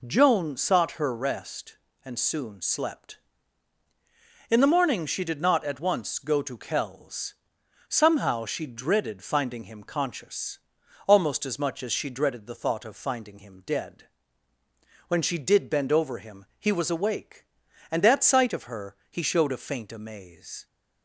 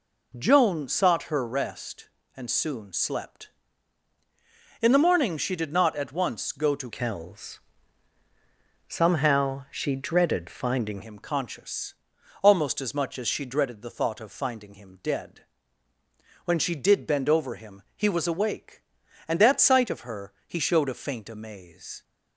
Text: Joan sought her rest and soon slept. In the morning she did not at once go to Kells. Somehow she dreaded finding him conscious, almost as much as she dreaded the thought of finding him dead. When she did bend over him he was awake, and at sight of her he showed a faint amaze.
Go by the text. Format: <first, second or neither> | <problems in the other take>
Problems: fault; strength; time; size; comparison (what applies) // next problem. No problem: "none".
first | changes voice from "Kells" to "finding"; from 6.9 to 11.0 s; 4.1 s long